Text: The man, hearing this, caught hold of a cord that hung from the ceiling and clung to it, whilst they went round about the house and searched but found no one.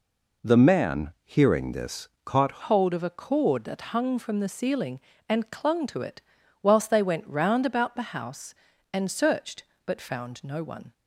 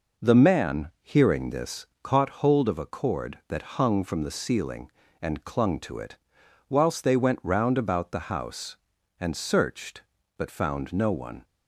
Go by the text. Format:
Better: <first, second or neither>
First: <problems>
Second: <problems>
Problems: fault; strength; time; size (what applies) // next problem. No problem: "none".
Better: second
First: changes voice at "hold"; from 2.6 s on; 8.3 s long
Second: none